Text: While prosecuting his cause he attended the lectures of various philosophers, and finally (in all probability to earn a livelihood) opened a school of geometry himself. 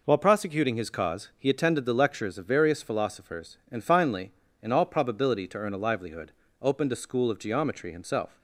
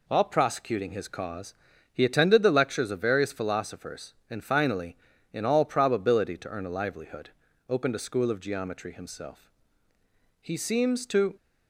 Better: first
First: none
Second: pauses between "cause" and "he"; at 1.5 s; 0.38 s long // goes on to say "He seems to"; noticeable; from 10.4 s on; 0.96 s long

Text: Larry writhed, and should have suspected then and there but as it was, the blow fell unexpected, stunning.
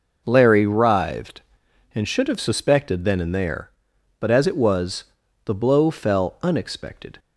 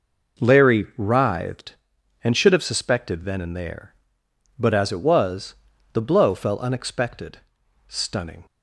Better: second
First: stops before "stunning"; at 7.1 s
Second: none

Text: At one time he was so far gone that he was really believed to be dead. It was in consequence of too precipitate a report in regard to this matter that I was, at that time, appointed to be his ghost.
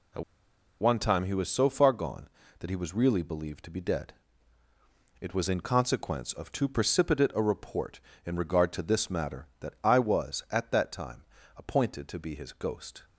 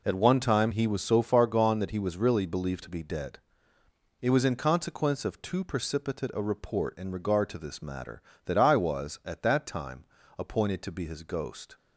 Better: second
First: pauses between "At" and "one"; noticeable; at 0.2 s; 0.57 s long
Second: none

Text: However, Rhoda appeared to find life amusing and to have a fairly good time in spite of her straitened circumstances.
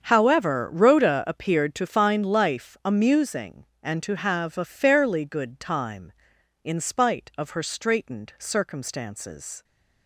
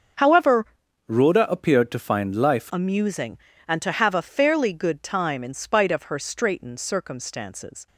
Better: first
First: starts louder than the rest; strong; until 1.0 s; 7.5 dB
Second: starts louder than the rest; until 1.5 s; 6.5 dB // changes voice from "Rhoda" to "life"; from 1.0 to 2.7 s; 1.7 s long

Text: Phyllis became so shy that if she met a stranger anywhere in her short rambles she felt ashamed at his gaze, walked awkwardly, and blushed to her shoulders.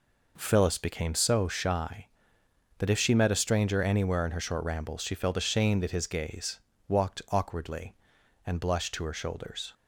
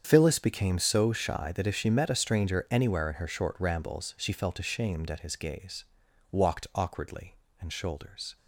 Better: first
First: none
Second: starts louder than the rest; strong; until 1.0 s; 8 dB // skips "blushed to her"; at 7.7 s

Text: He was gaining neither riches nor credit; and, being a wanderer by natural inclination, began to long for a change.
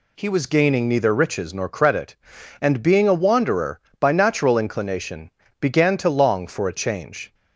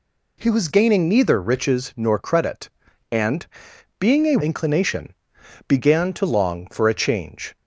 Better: first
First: none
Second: skips "wanderer by natural"; at 4.3 s

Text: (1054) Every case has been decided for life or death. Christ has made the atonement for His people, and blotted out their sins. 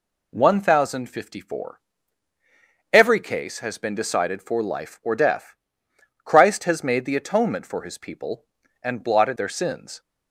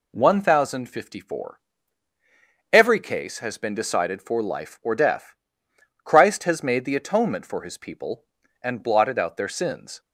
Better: second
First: skips "out"; at 9.3 s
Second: none

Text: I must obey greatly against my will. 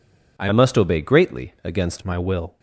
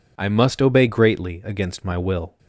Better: second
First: changes voice from "must" to "against"; from 0.5 to 2.0 s; 1.5 s long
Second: none

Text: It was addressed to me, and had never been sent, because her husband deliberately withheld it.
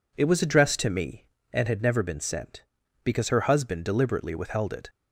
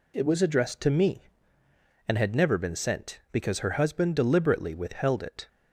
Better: neither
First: none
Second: none

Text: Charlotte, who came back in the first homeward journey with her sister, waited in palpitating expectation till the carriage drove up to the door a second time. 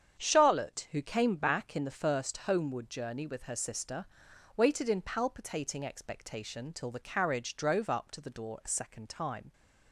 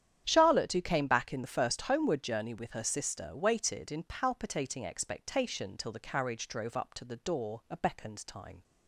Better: first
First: starts louder than the rest; strong; until 1.2 s; 8 dB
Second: starts louder than the rest; strong; until 1.2 s; 9.5 dB // says "beckoned" for "second"; at 7.7 s

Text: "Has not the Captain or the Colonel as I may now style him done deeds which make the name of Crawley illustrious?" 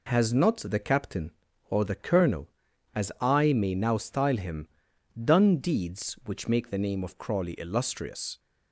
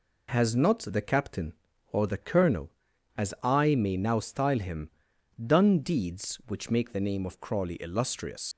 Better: first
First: pauses between "him" and "done"; noticeable; at 4.6 s; 0.52 s long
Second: pauses between "him" and "done"; noticeable; at 4.9 s; 0.52 s long // leaves "illustrious" unfinished; at 8.5 s; 100 ms

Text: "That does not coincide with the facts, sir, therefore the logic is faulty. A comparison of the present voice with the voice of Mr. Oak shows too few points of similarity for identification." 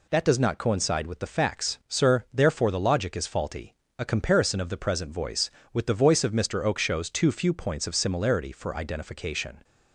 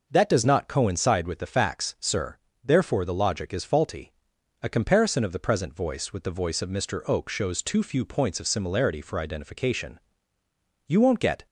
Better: first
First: none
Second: goes on to say "You won't get"; from 10.8 s on; 0.60 s long

